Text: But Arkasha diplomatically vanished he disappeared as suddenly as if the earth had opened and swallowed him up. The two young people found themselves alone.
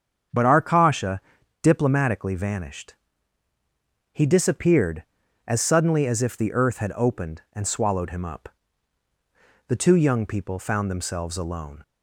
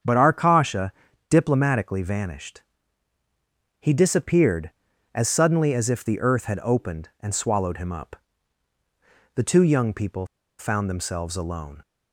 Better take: first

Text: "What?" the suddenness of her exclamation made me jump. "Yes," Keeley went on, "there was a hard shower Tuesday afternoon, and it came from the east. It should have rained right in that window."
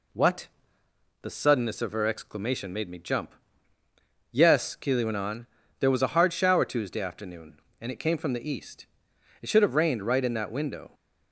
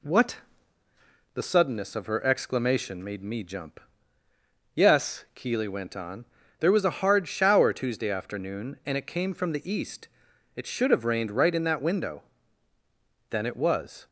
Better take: first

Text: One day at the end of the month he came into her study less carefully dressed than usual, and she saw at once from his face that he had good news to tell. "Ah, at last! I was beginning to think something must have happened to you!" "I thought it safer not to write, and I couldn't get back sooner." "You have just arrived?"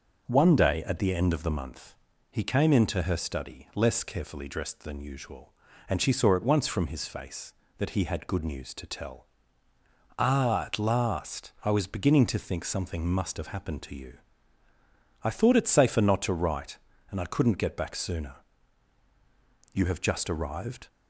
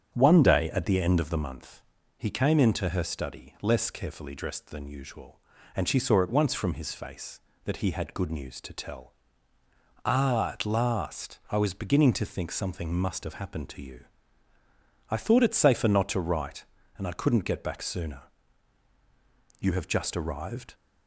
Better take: first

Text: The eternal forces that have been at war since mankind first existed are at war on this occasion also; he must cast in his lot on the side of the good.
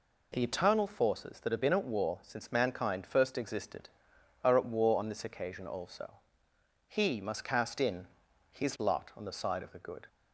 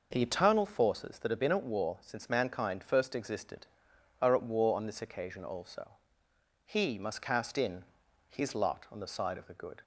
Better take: first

